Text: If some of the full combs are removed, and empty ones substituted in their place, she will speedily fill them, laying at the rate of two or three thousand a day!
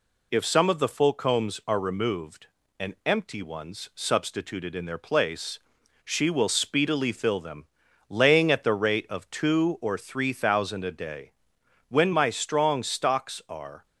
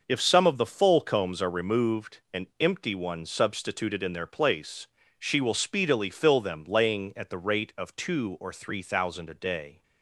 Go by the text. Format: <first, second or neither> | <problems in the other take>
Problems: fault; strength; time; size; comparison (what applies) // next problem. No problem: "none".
second | goes on to say "When my strong stocks are"; strong; from 11.8 s on; 1.9 s long